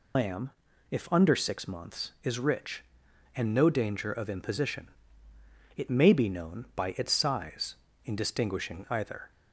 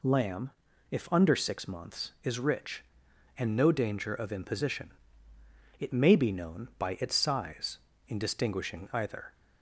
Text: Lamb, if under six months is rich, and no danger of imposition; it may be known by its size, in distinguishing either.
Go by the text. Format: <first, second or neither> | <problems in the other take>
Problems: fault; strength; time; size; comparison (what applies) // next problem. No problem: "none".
second | loses the start of "Lamb"; at 0.1 s; 120 ms